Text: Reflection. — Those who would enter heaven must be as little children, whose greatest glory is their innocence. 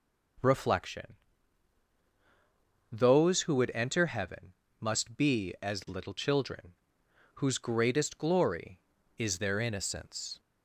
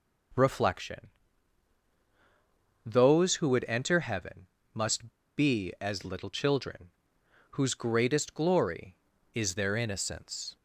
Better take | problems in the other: first | pauses between "heaven" and "must"; slight; at 4.4 s; 0.26 s long; slight in the first // pauses between "must" and "be"; slight; at 5.1 s; 0.25 s long

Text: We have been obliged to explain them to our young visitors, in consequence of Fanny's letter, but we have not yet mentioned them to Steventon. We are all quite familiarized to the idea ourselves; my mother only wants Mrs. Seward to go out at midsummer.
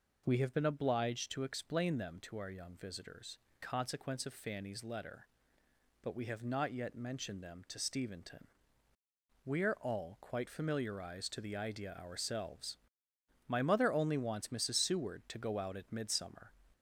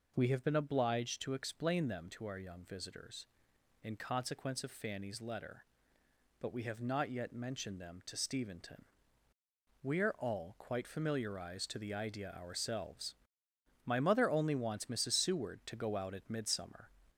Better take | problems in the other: second | skips "in"; at 3.4 s

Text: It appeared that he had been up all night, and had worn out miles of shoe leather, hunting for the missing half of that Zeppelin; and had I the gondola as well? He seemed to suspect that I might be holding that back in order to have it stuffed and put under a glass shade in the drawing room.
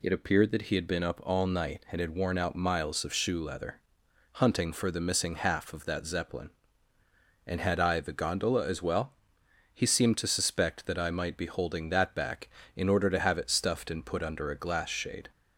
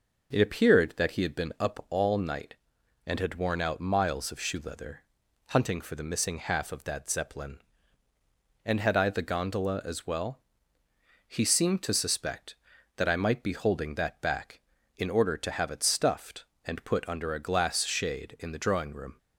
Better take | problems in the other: second | stops before "in the drawing room"; at 15.3 s

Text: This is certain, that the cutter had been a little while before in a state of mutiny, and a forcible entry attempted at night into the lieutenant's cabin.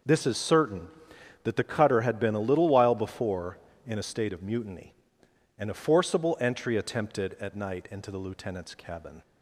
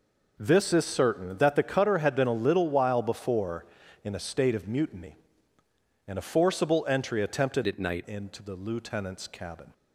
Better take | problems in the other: first | changes voice from "at" to "night"; from 7.6 to 8.0 s; 0.4 s long

